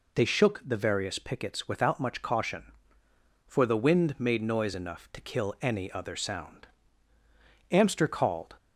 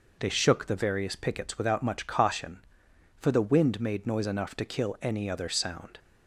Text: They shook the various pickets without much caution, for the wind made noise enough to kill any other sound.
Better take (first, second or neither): second